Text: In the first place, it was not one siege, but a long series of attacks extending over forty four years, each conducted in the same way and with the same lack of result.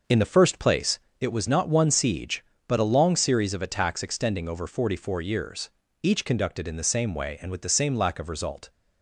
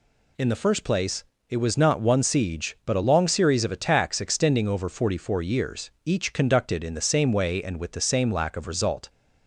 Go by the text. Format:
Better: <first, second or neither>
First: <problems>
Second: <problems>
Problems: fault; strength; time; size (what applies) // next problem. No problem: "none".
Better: second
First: starts louder than the rest; noticeable; until 1.0 s; 6 dB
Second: none